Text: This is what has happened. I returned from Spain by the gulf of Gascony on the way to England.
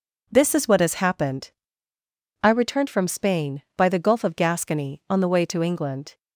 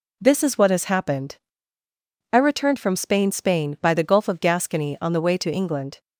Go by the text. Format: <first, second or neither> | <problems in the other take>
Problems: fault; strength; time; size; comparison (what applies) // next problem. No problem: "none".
first | says "Spain" twice; at 3.3 s